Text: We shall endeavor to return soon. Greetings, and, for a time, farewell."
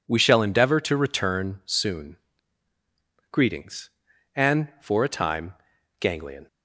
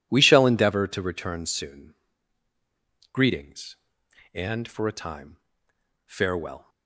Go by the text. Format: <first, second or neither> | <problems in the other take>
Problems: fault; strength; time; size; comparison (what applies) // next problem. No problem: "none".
second | says "ganglion" for "farewell"; at 5.9 s